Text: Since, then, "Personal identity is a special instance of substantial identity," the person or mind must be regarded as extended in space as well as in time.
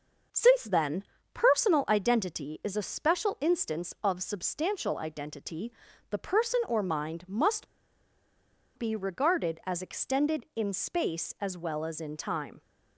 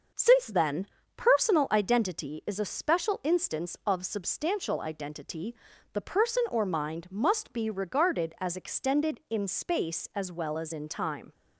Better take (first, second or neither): second